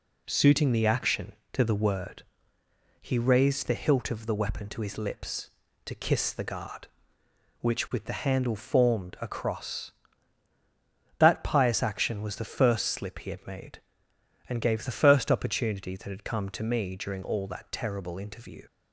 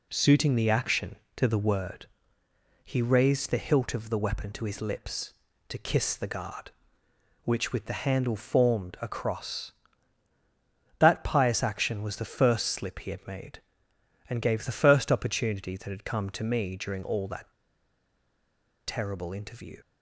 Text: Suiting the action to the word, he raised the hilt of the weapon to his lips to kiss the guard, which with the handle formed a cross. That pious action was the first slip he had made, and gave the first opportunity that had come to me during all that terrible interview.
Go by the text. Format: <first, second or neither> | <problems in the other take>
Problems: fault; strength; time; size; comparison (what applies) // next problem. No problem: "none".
first | pauses between "that" and "terrible"; strong; at 17.5 s; 1.3 s long